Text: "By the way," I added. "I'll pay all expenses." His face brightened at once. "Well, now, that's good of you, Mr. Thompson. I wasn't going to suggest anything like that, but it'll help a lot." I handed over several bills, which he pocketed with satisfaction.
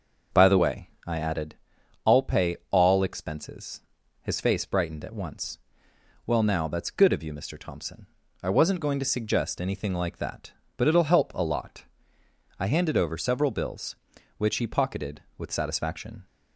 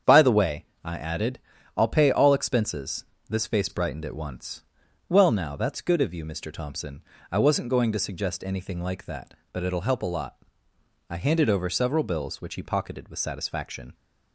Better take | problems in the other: first | starts louder than the rest; strong; until 1.2 s; 8 dB; noticeable in the first // says "This" for "His"; at 3.2 s

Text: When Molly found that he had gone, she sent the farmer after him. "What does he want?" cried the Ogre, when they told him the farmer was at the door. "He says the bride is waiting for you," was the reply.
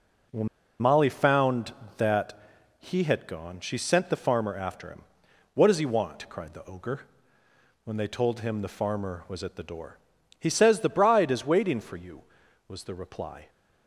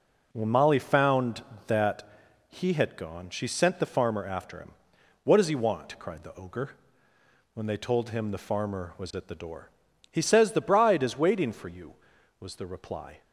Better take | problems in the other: second | pauses between "When" and "Molly"; slight; at 0.4 s; 0.32 s long // pauses between "that" and "he"; at 2.3 s; 0.38 s long; also in the second

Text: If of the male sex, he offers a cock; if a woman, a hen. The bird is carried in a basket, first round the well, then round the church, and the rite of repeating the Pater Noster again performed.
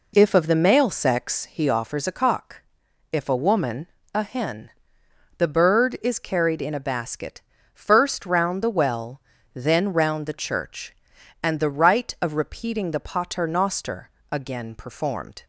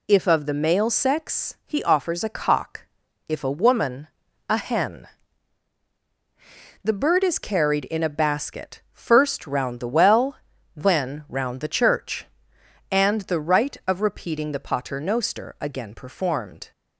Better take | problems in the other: second | starts louder than the rest; until 1.4 s; 3.5 dB // pauses between "Noster" and "again"; slight; at 14.0 s; 0.22 s long

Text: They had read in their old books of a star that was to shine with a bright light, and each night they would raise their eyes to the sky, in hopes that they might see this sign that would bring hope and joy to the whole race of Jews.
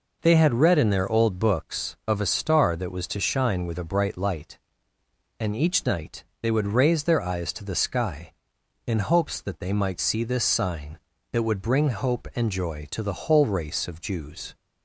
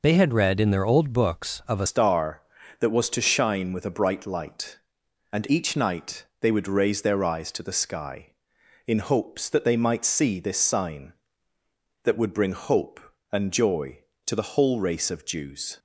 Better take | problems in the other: first | changes voice at "star"; from 1.8 s on; 13.9 s long // pauses between "night" and "they"; slight; at 6.2 s; 0.16 s long; slight in the first

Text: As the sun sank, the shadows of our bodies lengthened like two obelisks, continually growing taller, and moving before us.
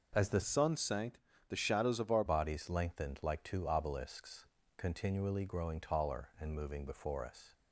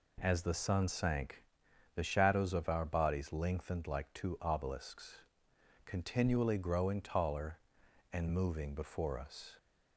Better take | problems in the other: second | changes voice from "sun" to "our"; from 0.4 to 2.2 s; 1.8 s long

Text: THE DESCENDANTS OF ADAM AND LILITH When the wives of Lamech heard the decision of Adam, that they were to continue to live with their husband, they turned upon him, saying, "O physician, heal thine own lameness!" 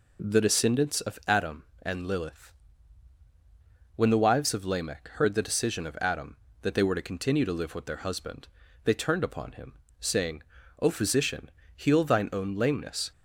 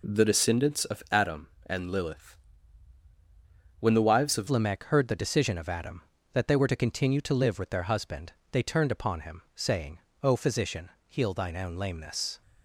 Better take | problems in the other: first | pauses between "LILITH" and "When"; strong; at 2.3 s; 1.4 s long; strong in the first // changes voice at "Lamech"; from 4.4 s on; 8.0 s long

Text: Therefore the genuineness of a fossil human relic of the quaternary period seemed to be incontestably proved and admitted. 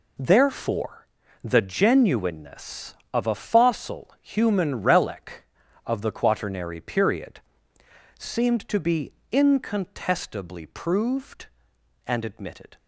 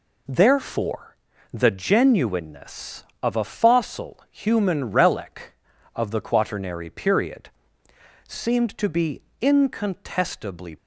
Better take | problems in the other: first | pauses between "Therefore" and "the"; slight; at 1.1 s; 0.36 s long; slight in the first // pauses between "period" and "seemed"; noticeable; at 7.4 s; 0.78 s long; noticeable in the first // pauses between "be" and "incontestably"; slight; at 9.2 s; 0.20 s long; slight in the first // stops before "proved and admitted"; at 10.7 s

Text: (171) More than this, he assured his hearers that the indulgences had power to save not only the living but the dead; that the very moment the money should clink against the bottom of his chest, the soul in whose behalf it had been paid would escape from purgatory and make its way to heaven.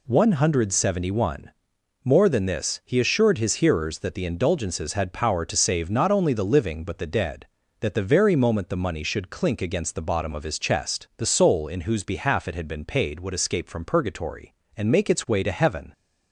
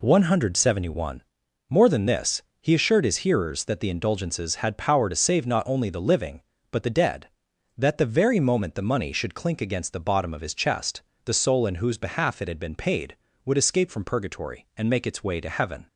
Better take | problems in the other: neither | none

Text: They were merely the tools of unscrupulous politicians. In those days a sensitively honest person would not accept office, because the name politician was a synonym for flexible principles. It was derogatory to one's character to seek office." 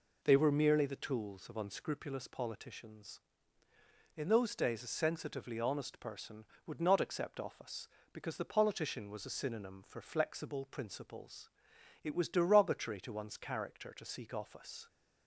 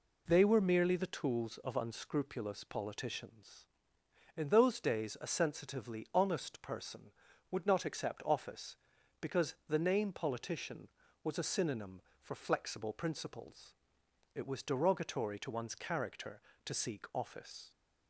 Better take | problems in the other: second | skips "name"; at 8.4 s

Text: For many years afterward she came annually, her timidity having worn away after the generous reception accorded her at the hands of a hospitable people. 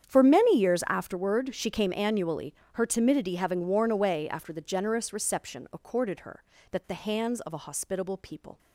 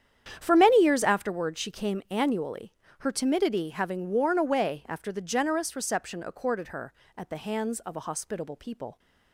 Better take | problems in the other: second | starts louder than the rest; strong; until 1.1 s; 8.5 dB; strong in the second // says "that" for "at"; at 6.7 s

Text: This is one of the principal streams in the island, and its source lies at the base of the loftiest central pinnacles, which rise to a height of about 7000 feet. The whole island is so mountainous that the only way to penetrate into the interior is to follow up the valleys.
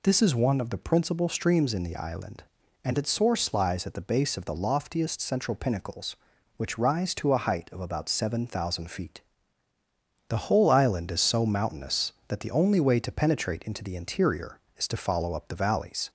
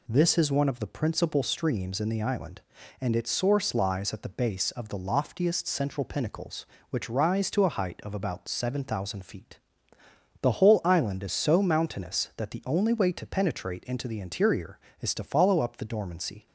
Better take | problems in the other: first | says "dormancy" for "valleys"; at 15.8 s

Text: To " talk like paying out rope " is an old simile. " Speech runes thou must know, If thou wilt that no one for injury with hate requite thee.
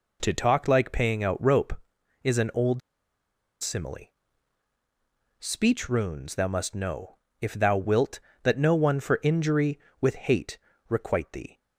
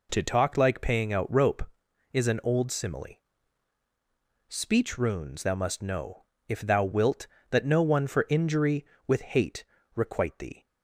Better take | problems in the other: second | pauses between "old" and "simile"; noticeable; at 2.8 s; 0.83 s long // pauses between "hate" and "requite"; slight; at 10.5 s; 0.30 s long; slight in the second

